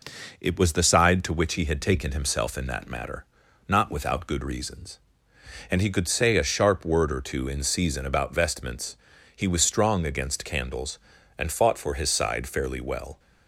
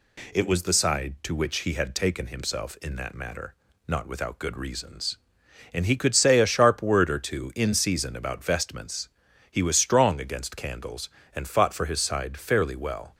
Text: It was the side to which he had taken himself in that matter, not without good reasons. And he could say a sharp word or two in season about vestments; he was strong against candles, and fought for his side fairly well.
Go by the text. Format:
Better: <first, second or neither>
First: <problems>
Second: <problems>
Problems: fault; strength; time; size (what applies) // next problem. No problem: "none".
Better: neither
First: none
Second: none